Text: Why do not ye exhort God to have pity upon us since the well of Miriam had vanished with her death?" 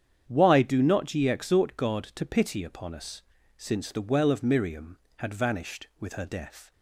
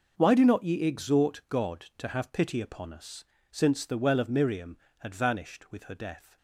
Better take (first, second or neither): second